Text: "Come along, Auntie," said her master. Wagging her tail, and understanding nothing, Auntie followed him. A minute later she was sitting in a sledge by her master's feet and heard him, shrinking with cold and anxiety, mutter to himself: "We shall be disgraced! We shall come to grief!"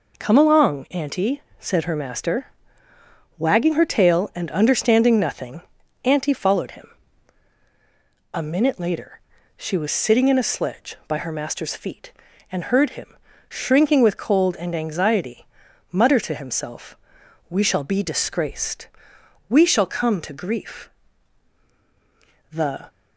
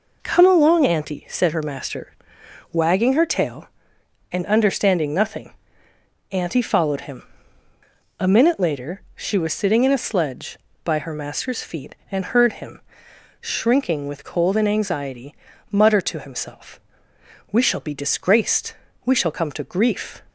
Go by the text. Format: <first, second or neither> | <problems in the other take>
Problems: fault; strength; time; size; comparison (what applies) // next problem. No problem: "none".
second | pauses between "later" and "she"; at 9.1 s; 0.36 s long; slight in the second // goes on to say "The"; slight; from 22.5 s on; 0.38 s long